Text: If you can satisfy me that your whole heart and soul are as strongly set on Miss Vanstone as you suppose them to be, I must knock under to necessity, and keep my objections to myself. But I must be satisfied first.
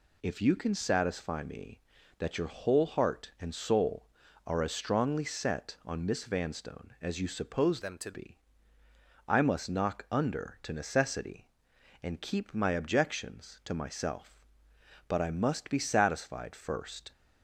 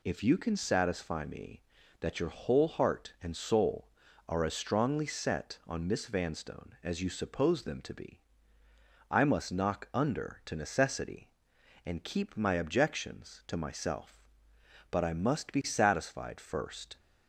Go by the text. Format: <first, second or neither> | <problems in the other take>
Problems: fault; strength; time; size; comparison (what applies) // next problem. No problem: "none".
second | changes voice from "them" to "to"; from 7.8 to 8.1 s; 0.3 s long